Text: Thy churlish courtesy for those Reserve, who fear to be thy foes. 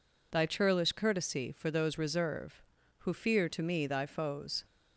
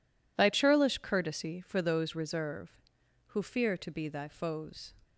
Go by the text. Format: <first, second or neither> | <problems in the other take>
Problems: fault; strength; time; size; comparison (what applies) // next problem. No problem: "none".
second | says "me" for "be"; at 3.6 s